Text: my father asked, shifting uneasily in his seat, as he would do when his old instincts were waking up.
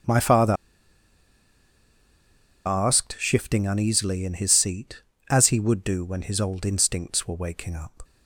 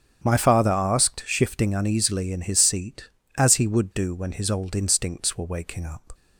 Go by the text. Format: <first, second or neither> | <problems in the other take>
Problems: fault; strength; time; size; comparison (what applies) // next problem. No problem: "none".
second | starts louder than the rest; strong; until 3.2 s; 8.5 dB; strong in the second // pauses between "father" and "asked"; strong; at 0.5 s; 2.1 s long